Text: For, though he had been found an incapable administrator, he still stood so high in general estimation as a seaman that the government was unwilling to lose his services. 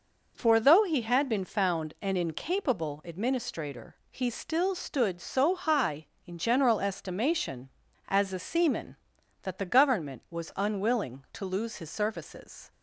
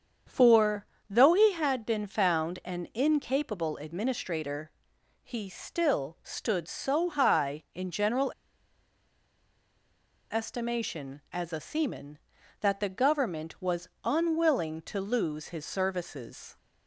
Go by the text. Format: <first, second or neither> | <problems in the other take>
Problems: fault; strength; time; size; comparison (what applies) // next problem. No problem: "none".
first | starts louder than the rest; strong; until 1.5 s; 7.5 dB // pauses between "general" and "estimation"; strong; at 8.3 s; 1.9 s long // pauses between "was" and "unwilling"; slight; at 13.8 s; 0.16 s long